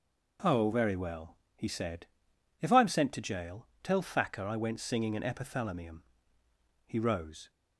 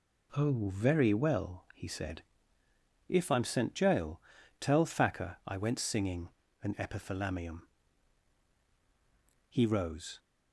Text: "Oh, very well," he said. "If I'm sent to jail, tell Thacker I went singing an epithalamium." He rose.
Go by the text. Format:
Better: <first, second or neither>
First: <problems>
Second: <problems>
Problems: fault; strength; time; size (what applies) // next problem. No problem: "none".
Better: first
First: none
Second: skips "to"; at 3.7 s // pauses between "singing" and "an"; slight; at 6.2 s; 0.32 s long